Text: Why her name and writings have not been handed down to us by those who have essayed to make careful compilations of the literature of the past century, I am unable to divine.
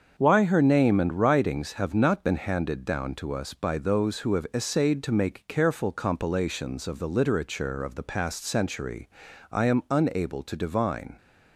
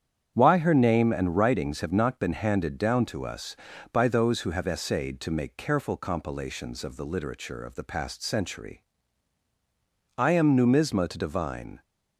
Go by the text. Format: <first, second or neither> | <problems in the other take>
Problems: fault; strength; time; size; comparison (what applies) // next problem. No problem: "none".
first | starts louder than the rest; strong; until 1.3 s; 8.5 dB; also in the first // says "numisma" for "unable"; at 10.5 s